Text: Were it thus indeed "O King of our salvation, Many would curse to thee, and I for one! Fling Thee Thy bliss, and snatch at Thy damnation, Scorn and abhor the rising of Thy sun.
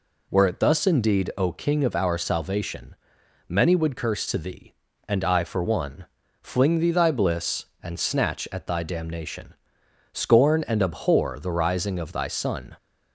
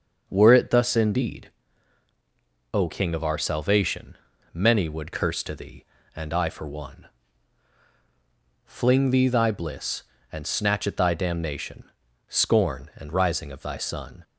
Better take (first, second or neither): first